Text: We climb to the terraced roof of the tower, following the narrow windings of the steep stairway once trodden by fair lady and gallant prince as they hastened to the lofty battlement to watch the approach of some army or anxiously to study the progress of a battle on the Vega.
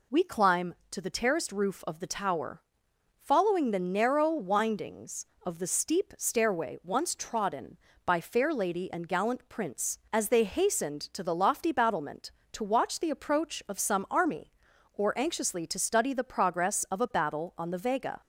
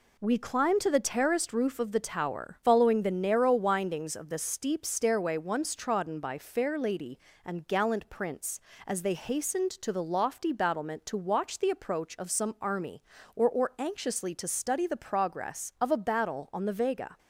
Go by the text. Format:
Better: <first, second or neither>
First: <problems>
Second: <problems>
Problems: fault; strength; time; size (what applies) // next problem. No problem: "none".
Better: first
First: none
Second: says "or" twice; at 13.4 s